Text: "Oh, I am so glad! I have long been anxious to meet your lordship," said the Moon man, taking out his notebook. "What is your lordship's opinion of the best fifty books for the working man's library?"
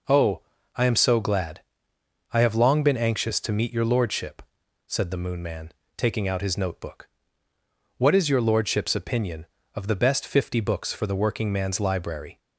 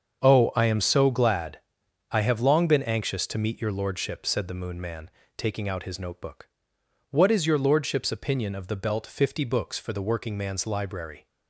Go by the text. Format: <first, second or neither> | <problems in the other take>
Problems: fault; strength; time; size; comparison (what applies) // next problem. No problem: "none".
first | starts louder than the rest; strong; until 1.2 s; 7 dB // says "belt" for "best"; at 8.7 s